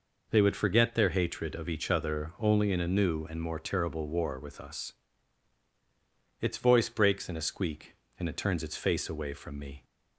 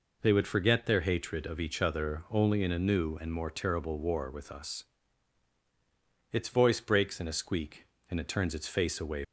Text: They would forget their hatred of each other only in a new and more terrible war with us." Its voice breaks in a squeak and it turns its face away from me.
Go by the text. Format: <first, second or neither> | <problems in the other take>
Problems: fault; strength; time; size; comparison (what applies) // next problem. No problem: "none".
first | stops before "from me"; at 9.2 s